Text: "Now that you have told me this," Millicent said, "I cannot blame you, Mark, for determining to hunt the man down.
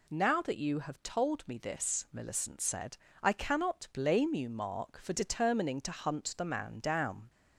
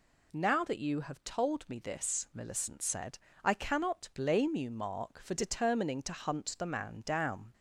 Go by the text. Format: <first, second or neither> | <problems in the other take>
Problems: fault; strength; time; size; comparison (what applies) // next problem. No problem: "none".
neither | none